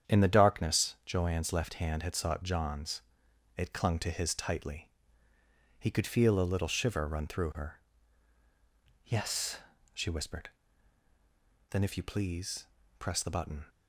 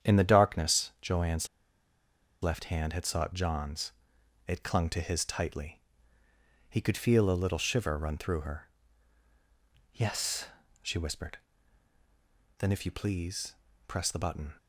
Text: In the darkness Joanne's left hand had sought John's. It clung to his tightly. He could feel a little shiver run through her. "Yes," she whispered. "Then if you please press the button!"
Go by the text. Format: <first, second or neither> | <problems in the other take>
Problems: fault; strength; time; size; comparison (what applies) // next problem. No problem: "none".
first | starts louder than the rest; strong; until 1.1 s; 8.5 dB; strong in the first // pauses between "Joanne's" and "left"; noticeable; at 1.4 s; 0.95 s long // pauses between "please" and "press"; slight; at 13.5 s; 0.32 s long; slight in the first